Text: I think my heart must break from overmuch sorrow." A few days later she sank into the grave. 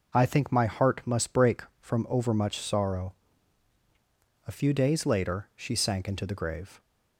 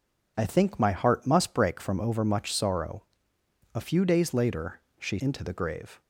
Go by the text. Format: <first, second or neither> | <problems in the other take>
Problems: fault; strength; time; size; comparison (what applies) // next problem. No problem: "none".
first | pauses between "later" and "she"; slight; at 4.7 s; 0.18 s long // skips "sank"; at 5.1 s